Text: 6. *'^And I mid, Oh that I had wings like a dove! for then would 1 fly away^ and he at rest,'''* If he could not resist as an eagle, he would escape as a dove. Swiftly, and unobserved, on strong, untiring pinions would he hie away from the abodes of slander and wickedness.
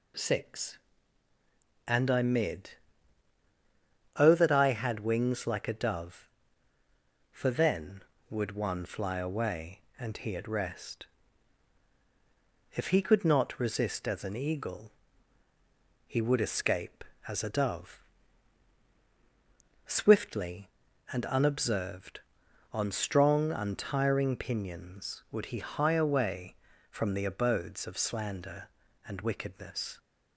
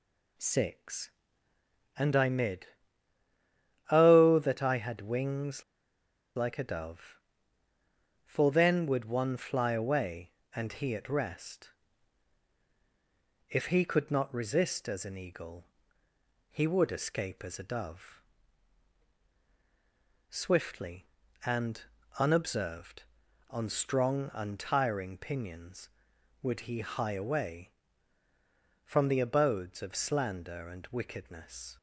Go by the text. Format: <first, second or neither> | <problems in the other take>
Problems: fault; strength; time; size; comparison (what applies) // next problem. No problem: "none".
first | pauses between "wings" and "like"; noticeable; at 5.6 s; 0.73 s long // pauses between "and" and "unobserved"; at 21.8 s; 0.38 s long